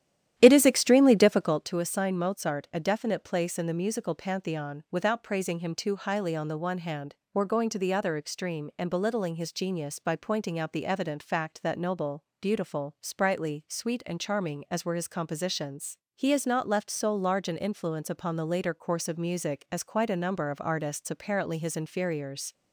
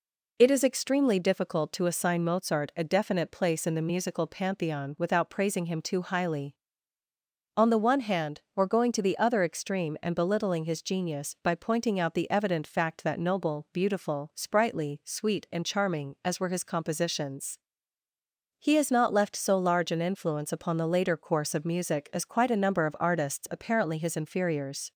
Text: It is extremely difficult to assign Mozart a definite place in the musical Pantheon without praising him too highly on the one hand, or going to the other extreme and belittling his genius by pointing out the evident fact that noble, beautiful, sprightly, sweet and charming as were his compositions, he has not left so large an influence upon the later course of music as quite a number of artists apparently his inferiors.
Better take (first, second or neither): second